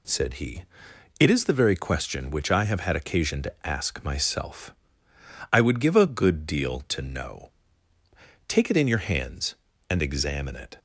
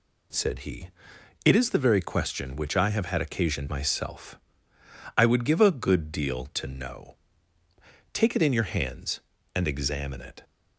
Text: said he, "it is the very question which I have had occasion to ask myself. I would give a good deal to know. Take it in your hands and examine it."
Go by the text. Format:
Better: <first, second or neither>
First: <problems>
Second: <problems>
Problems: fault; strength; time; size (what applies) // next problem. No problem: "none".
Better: first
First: none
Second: skips "to ask"; at 3.6 s